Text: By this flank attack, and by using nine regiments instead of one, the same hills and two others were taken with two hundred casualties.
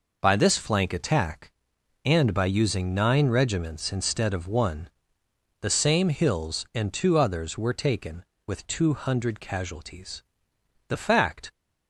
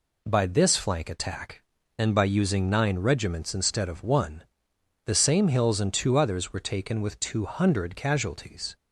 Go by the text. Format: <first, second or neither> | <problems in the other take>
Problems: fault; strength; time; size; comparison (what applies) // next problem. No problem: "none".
second | goes on to say "The fact"; noticeable; from 10.8 s on; 0.62 s long